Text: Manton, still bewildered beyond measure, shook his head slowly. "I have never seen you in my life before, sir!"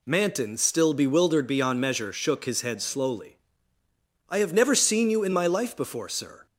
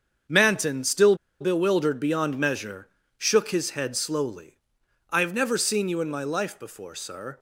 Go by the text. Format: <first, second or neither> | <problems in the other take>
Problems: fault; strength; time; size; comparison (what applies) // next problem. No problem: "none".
first | starts louder than the rest; strong; until 1.5 s; 7.5 dB // pauses between "still" and "bewildered"; slight; at 1.1 s; 0.25 s long